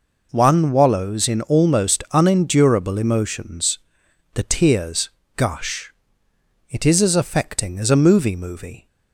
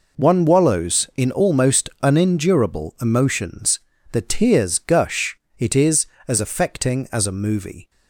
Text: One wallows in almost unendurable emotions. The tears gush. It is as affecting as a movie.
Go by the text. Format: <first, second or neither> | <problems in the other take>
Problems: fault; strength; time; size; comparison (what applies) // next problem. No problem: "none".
second | pauses between "tears" and "gush"; slight; at 5.1 s; 0.26 s long // says "movie" twice; at 8.3 s